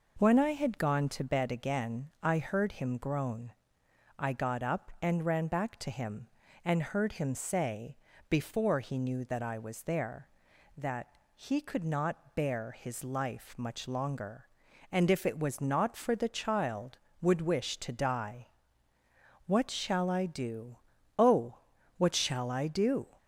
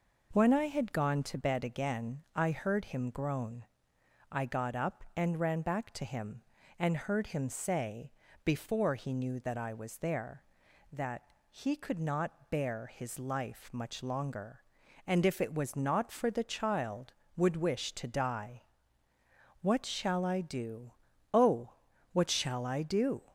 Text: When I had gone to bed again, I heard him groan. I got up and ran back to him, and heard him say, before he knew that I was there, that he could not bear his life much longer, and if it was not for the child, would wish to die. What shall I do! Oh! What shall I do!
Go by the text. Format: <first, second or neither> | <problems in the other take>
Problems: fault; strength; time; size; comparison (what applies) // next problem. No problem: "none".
neither | pauses between "that" and "he"; slight; the same in both